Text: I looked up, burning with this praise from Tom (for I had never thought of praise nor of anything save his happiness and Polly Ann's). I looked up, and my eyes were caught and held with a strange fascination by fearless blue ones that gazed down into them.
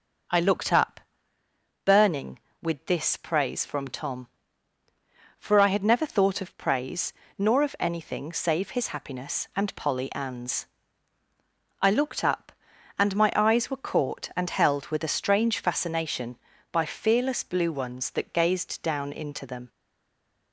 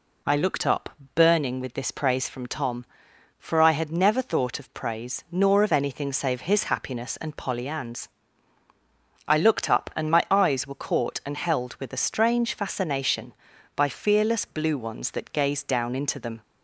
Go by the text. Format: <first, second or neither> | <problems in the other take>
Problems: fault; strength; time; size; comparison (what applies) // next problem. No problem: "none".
second | pauses between "praise" and "nor"; slight; at 7.1 s; 0.24 s long // stays silent after the last word; slight; from 19.6 s on; 0.9 s long